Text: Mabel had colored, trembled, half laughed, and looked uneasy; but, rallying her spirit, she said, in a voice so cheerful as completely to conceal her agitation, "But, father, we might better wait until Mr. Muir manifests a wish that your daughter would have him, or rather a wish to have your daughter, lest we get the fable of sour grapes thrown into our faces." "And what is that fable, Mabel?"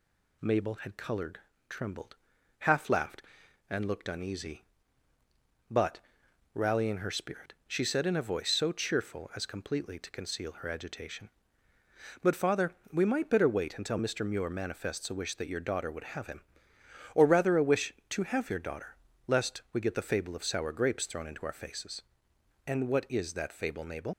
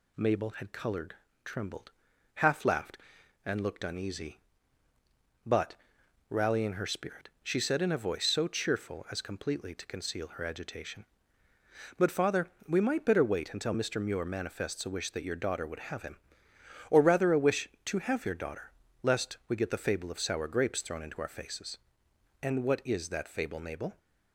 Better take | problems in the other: second | leaves "Mabel" unfinished; at 24.1 s; 85 ms

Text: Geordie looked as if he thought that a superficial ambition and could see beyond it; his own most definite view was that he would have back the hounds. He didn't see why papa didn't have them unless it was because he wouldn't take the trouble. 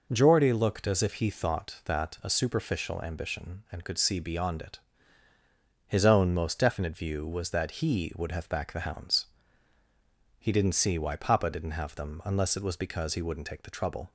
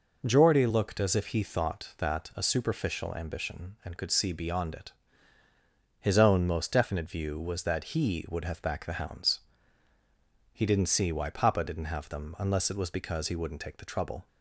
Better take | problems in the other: neither | none

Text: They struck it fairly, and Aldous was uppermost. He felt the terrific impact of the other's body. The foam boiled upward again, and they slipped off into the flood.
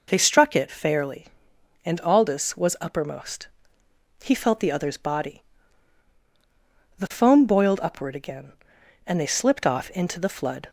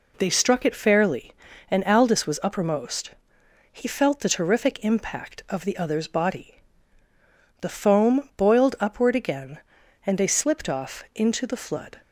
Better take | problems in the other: second | skips "terrific impact of the"; at 4.7 s

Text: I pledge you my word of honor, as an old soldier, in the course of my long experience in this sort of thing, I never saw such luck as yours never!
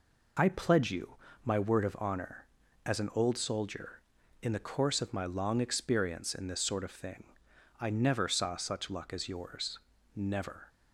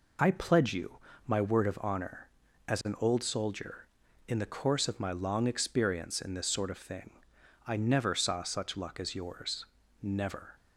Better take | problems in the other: neither | pauses between "you" and "my"; slight; the same in both // pauses between "yours" and "never"; slight; the same in both

